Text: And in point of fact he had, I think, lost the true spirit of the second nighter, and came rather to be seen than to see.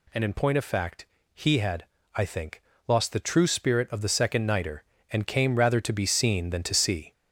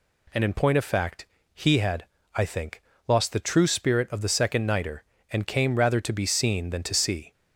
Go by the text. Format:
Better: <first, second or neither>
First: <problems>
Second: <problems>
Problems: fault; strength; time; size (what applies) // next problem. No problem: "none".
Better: second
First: gets louder; noticeable; throughout; 4 dB // pauses between "fact" and "he"; slight; at 1.0 s; 0.28 s long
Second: pauses between "fact" and "he"; slight; at 1.2 s; 0.28 s long